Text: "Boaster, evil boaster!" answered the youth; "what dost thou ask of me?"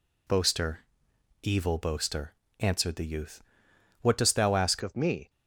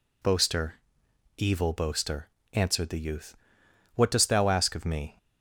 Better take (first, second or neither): second